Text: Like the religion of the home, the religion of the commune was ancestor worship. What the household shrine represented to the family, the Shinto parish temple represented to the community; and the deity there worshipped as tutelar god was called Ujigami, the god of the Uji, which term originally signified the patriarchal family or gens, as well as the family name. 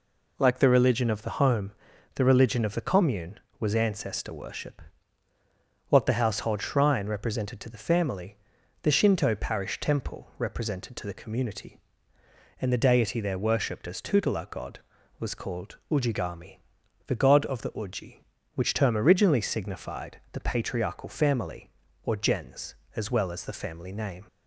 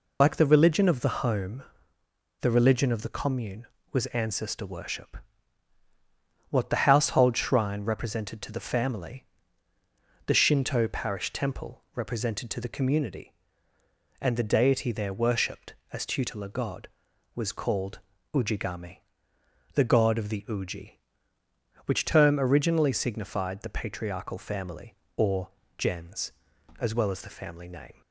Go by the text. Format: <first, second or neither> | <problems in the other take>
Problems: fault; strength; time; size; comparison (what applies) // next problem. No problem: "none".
first | loses the start of "Like"; at 0.2 s; 90 ms // pauses between "called" and "Ujigami"; slight; at 18.0 s; 0.34 s long // pauses between "or" and "gens"; slight; at 25.5 s; 0.26 s long